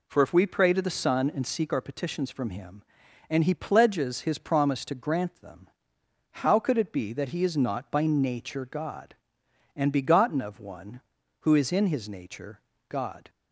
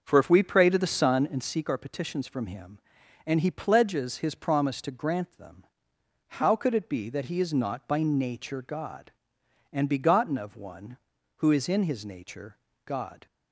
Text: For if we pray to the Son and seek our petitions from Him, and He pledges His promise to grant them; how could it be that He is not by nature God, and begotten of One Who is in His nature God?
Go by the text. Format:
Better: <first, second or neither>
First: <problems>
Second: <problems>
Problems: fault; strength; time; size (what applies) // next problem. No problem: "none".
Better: first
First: pauses between "nature" and "God"; slight; at 12.6 s; 0.26 s long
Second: starts louder than the rest; until 1.3 s; 6.5 dB // pauses between "nature" and "God"; slight; at 12.5 s; 0.26 s long